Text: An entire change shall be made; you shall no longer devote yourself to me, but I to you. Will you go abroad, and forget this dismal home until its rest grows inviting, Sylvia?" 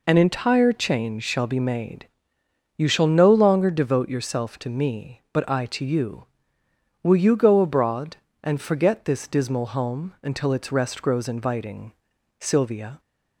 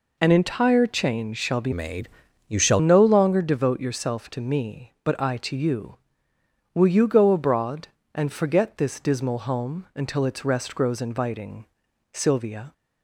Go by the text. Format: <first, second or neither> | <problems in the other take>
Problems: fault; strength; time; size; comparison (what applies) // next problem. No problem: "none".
first | changes voice from "made" to "shall"; from 1.7 to 2.7 s; 1.0 s long